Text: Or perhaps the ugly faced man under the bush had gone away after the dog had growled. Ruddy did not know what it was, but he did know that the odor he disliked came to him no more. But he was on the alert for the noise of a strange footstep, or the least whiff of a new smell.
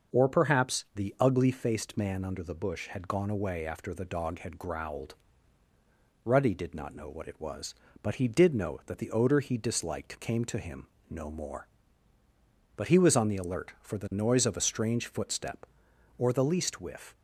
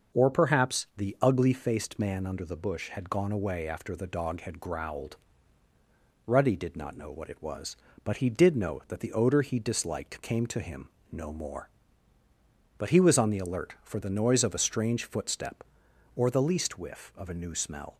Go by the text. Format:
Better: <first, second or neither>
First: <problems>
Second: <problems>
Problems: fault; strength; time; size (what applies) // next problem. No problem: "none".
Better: second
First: starts louder than the rest; until 1.2 s; 6.5 dB // pauses between "him" and "no"; slight; at 10.8 s; 0.22 s long // stops before "of a new smell"; at 17.1 s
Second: starts louder than the rest; until 1.2 s; 6.5 dB // pauses between "him" and "no"; slight; at 10.8 s; 0.22 s long